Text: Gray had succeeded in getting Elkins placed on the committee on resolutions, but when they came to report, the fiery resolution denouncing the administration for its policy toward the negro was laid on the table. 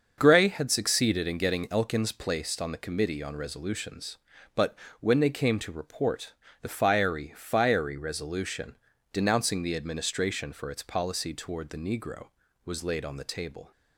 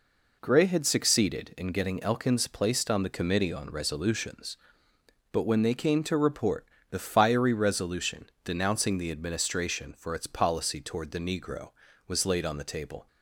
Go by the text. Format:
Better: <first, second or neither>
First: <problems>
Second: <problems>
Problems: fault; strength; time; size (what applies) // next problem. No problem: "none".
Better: second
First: starts louder than the rest; until 1.1 s; 6.5 dB // pauses between "but" and "when"; slight; at 4.7 s; 0.24 s long // says "fiery" twice; at 7.3 s // pauses between "resolution" and "denouncing"; at 8.7 s; 0.38 s long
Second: pauses between "resolution" and "denouncing"; slight; at 8.2 s; 0.16 s long